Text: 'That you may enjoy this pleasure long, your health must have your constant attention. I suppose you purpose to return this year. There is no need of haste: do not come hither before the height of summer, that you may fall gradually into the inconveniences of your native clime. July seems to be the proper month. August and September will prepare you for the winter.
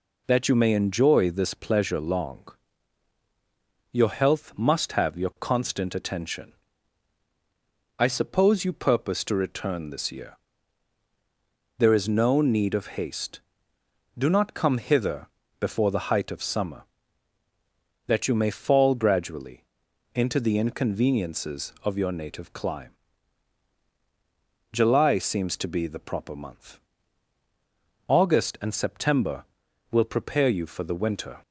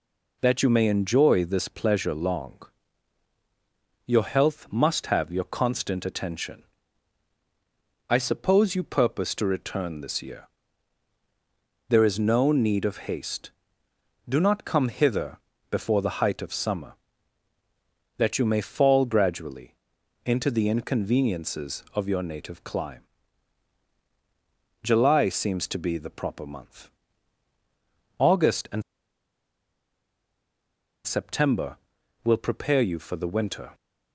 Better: first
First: pauses between "hither" and "before"; slight; at 15.2 s; 0.32 s long // pauses between "gradually" and "into"; noticeable; at 19.6 s; 0.52 s long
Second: pauses between "hither" and "before"; slight; at 15.3 s; 0.32 s long // pauses between "gradually" and "into"; noticeable; at 19.7 s; 0.52 s long // pauses between "and" and "September"; strong; at 28.8 s; 2.2 s long

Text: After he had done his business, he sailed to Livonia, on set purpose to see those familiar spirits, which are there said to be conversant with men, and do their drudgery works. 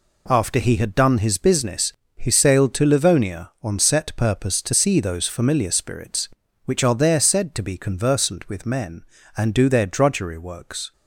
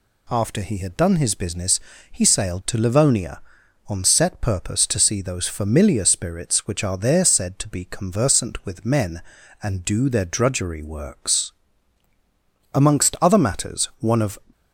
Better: first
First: none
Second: goes on to say "Amongst other matters one of"; strong; from 12.7 s on; 1.6 s long

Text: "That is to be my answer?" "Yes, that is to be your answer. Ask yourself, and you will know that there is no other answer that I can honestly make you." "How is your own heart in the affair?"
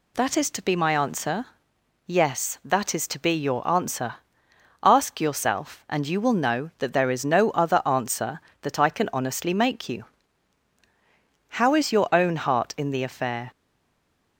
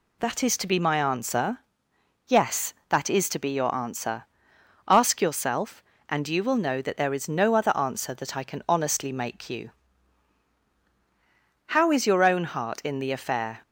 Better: second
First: stays silent after the last word; slight; from 13.5 s on; 0.8 s long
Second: none

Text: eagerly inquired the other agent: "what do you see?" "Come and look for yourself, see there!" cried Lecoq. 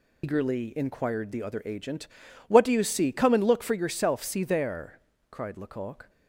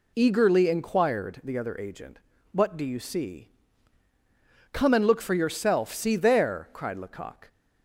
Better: second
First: loses the start of "eagerly"; at 0.2 s; 115 ms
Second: none

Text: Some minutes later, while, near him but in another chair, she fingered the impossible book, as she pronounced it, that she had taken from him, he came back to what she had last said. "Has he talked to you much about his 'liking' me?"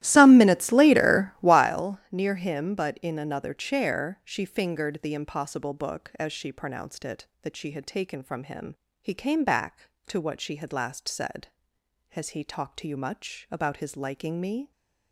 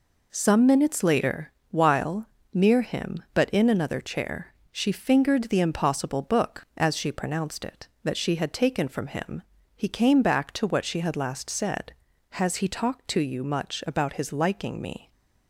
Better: second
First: starts louder than the rest; strong; until 1.7 s; 14.5 dB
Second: none

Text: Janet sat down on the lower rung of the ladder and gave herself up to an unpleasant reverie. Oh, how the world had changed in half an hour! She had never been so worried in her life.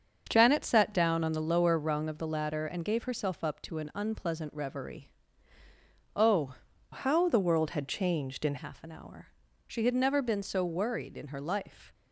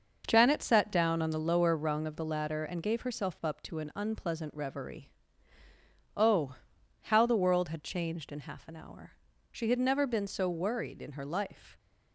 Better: second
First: starts louder than the rest; until 1.3 s; 6.5 dB // changes voice from "how" to "in"; from 6.9 to 8.5 s; 1.6 s long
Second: starts louder than the rest; noticeable; until 1.2 s; 6 dB

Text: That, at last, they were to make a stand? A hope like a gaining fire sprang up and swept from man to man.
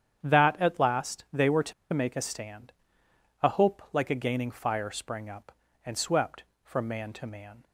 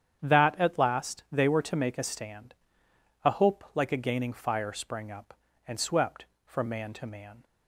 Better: second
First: starts louder than the rest; strong; until 1.2 s; 9 dB // pauses between "to" and "make"; slight; at 1.7 s; 0.20 s long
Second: starts louder than the rest; strong; until 1.2 s; 9 dB

